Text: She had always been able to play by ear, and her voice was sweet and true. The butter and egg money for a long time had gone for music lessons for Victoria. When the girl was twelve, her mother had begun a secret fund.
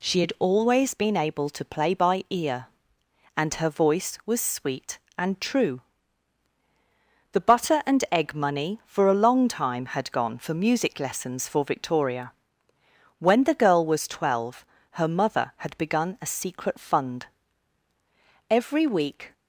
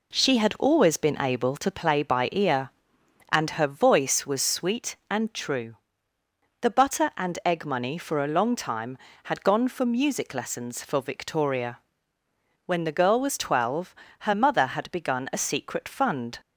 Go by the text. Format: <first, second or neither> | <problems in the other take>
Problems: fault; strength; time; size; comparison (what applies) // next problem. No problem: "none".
second | goes on to say "Every week"; noticeable; from 18.4 s on; 0.84 s long